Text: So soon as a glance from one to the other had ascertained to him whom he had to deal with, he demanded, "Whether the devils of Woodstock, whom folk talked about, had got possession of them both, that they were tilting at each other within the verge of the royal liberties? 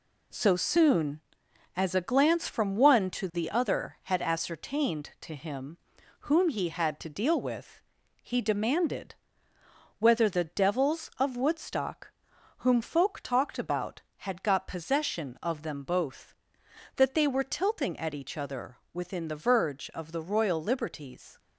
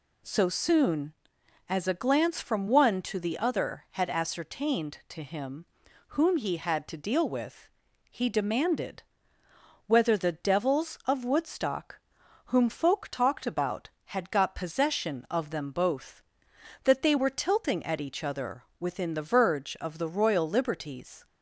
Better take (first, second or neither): second